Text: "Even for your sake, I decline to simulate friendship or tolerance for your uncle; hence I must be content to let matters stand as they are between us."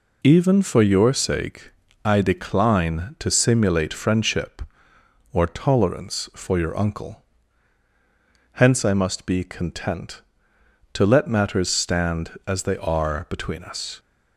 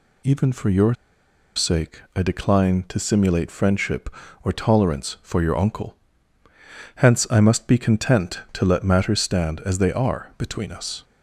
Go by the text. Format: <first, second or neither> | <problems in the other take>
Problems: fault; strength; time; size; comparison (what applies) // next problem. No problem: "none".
first | pauses between "your" and "sake"; noticeable; at 0.9 s; 0.62 s long